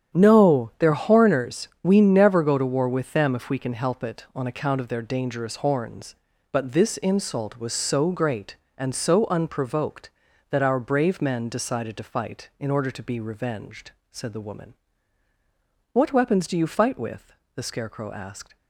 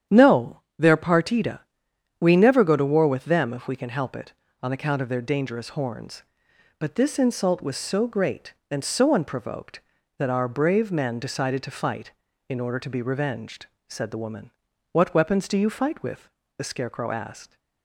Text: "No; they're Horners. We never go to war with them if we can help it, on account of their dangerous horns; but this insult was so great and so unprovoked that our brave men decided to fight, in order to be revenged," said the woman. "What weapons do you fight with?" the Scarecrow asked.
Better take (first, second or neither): first